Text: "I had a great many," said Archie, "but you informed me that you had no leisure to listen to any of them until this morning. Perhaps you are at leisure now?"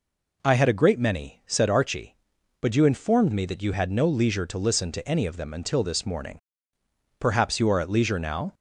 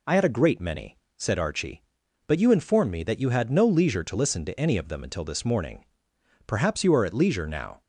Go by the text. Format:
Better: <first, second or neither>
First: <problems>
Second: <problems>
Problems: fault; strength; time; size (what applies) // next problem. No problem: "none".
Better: neither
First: none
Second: none